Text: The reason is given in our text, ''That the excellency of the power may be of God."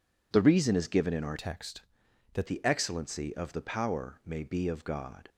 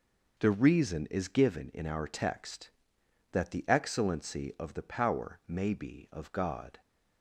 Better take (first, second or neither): second